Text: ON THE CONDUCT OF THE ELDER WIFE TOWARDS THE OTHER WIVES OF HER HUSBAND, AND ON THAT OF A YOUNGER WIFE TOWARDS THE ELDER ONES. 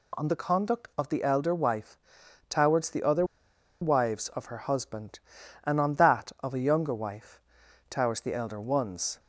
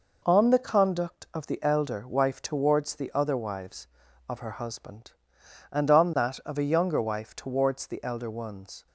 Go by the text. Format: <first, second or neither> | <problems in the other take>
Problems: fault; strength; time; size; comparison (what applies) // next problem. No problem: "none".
second | pauses between "WIFE" and "TOWARDS"; noticeable; at 1.9 s; 0.50 s long // pauses between "OTHER" and "WIVES"; noticeable; at 3.2 s; 0.55 s long // pauses between "WIFE" and "TOWARDS"; noticeable; at 7.4 s; 0.48 s long